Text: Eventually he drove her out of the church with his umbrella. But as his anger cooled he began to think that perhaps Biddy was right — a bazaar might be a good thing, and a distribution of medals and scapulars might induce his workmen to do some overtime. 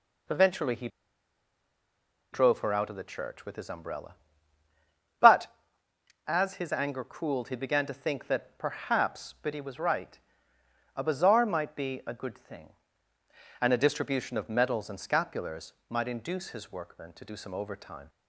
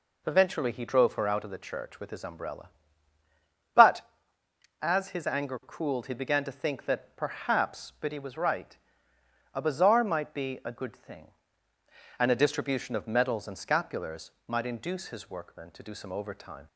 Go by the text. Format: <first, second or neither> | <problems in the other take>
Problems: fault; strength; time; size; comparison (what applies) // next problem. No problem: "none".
second | pauses between "he" and "drove"; strong; at 0.8 s; 1.4 s long // pauses between "scapulars" and "might"; slight; at 15.7 s; 0.16 s long; slight in the second